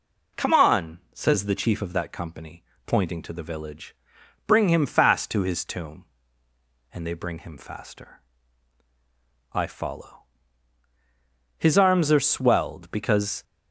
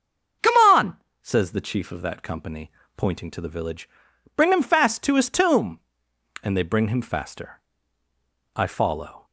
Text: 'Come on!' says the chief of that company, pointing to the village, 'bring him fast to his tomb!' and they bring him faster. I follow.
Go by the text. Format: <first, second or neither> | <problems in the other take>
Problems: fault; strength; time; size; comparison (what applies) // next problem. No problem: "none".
second | goes on to say "His arms are swelled because"; strong; from 11.5 s on; 1.8 s long